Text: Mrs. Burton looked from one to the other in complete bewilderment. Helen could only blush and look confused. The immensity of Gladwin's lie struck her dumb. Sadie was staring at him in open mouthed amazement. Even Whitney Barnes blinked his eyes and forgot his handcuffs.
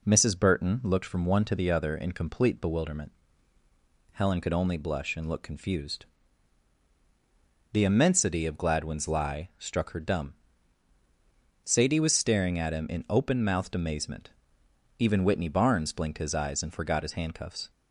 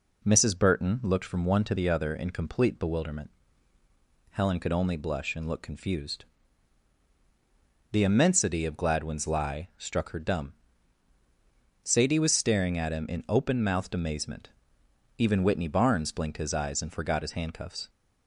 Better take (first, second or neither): neither